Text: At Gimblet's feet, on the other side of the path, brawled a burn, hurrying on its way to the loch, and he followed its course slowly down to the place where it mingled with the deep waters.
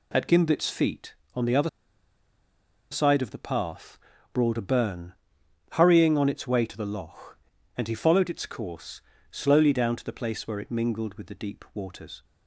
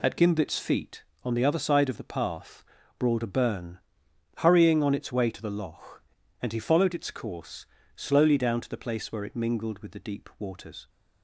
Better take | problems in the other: second | pauses between "other" and "side"; at 1.6 s; 1.2 s long // pauses between "course" and "slowly"; slight; at 9.0 s; 0.30 s long; slight in the second

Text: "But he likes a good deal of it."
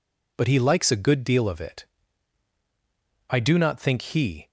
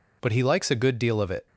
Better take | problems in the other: second | goes on to say "I do not think he"; noticeable; from 3.2 s on; 1.2 s long

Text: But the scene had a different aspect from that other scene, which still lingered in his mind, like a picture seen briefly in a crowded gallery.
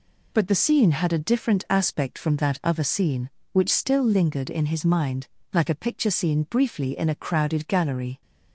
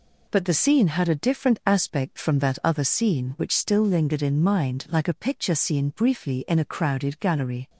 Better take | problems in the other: first | skips "his"; at 4.4 s

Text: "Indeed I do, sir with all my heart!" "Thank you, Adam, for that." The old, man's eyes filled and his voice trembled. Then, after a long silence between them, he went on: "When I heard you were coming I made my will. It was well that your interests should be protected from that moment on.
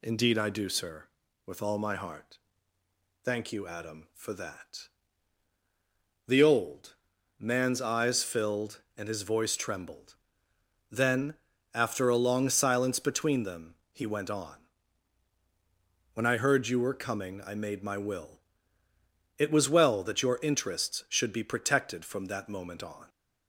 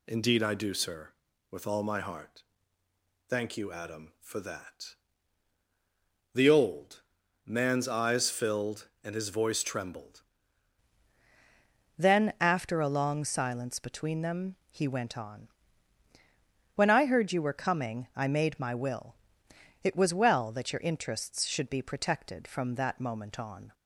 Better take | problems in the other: first | changes voice at "Then"; from 11.9 s on; 11.8 s long

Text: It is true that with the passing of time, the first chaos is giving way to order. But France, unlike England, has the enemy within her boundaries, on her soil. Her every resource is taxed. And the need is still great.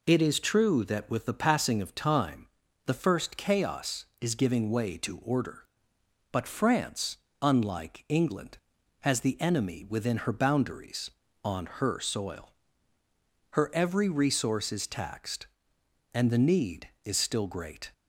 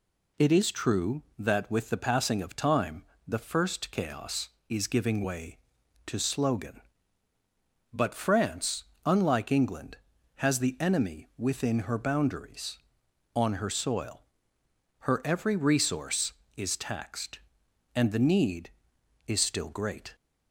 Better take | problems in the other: first | says "slogan" for "order"; at 6.1 s

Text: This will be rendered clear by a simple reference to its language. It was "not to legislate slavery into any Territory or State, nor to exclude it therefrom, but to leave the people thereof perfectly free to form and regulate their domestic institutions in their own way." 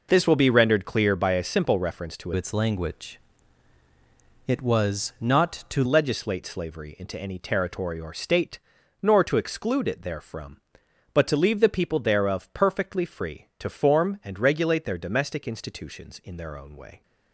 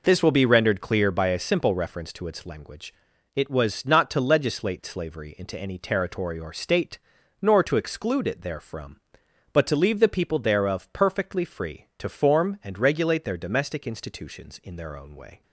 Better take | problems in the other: second | changes voice from "its" to "to"; from 2.3 to 5.8 s; 3.5 s long

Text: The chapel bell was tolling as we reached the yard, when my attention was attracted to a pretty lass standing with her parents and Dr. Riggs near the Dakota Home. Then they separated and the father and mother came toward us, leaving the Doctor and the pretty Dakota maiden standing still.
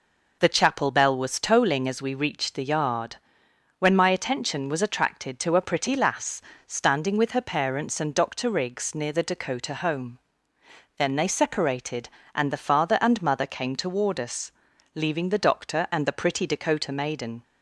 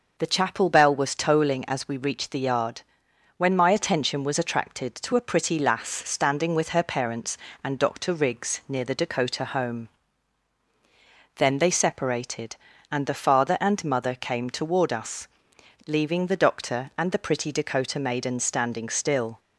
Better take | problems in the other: second | pauses between "lass" and "standing"; slight; at 6.4 s; 0.26 s long // stops before "standing still"; at 17.4 s

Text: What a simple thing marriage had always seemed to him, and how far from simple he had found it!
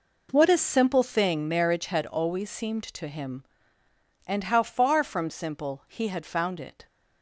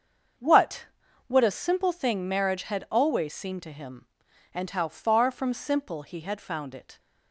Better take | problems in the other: first | starts louder than the rest; until 1.8 s; 7 dB // says "What" twice; at 1.2 s

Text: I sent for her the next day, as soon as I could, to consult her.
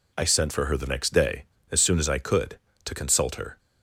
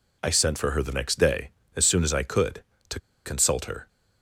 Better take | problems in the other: first | pauses between "to" and "consult"; slight; at 2.9 s; 0.26 s long

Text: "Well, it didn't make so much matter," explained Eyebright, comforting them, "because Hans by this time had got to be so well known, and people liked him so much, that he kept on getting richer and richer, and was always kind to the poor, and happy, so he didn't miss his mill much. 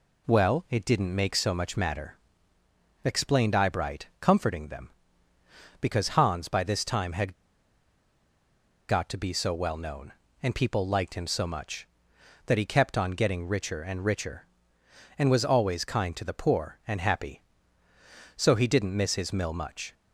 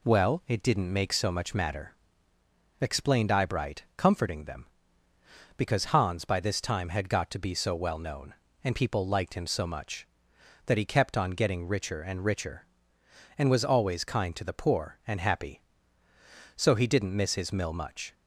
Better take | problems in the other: second | pauses between "had" and "got"; strong; at 7.3 s; 1.5 s long

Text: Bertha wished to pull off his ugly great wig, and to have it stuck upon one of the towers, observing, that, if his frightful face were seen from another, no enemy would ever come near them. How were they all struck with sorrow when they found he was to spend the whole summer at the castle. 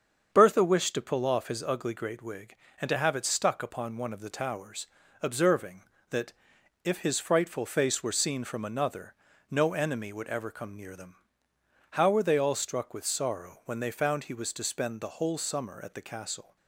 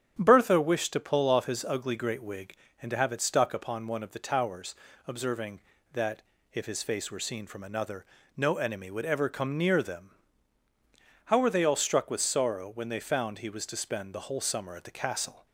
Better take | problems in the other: first | starts louder than the rest; strong; until 1.2 s; 9 dB; strong in the first // skips "frightful"; at 6.8 s

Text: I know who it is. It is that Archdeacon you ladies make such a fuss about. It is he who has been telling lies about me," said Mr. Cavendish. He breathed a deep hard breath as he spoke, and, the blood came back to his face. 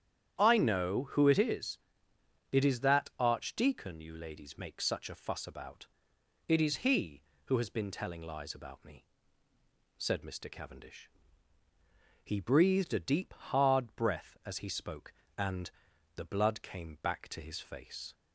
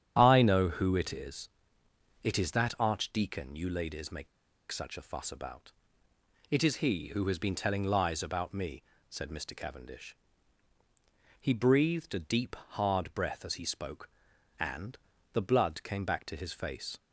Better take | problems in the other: first | starts louder than the rest; strong; until 1.1 s; 9.5 dB; strong in the first // pauses between "make" and "such"; at 4.2 s; 0.44 s long

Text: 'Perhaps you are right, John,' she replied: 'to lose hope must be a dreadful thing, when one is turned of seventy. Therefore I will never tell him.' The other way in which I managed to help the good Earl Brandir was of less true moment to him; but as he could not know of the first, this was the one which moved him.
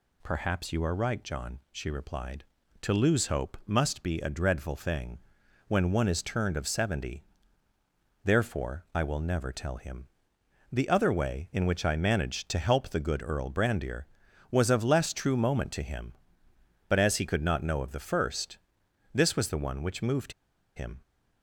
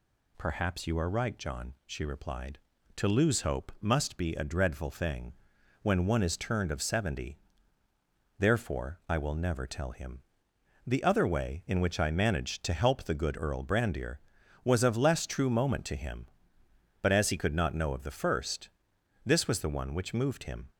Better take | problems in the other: second | pauses between "moved" and "him"; at 20.3 s; 0.43 s long

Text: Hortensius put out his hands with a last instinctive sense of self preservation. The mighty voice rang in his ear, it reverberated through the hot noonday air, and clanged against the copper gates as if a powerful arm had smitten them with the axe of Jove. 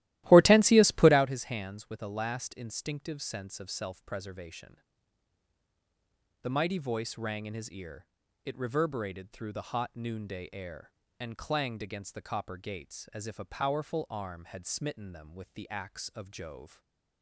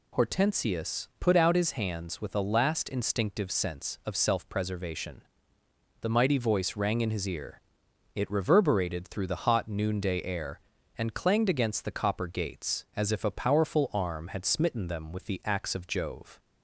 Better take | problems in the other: second | starts louder than the rest; strong; until 1.3 s; 15.5 dB // stays silent after the last word; slight; from 16.6 s on; 0.6 s long

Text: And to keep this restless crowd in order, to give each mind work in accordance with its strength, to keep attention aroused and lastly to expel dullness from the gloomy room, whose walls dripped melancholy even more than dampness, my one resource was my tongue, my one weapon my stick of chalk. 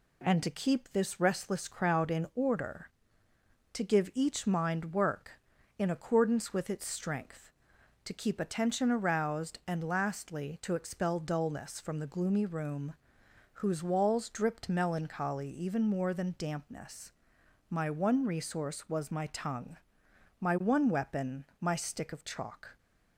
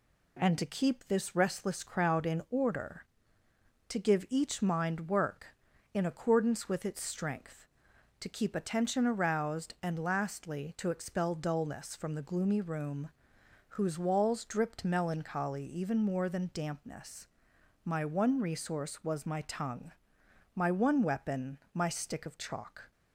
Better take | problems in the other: neither | pauses between "weapon" and "my"; slight; the same in both

